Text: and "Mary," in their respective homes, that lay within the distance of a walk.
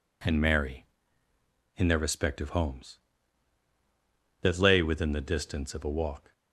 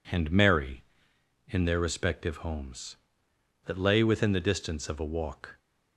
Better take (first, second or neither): neither